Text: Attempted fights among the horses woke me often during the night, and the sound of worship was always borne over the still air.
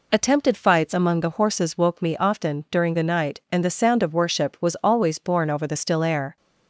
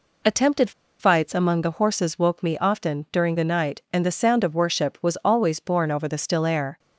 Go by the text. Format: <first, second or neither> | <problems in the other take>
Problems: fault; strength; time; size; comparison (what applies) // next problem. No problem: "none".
first | pauses between "Attempted" and "fights"; slight; at 0.7 s; 0.29 s long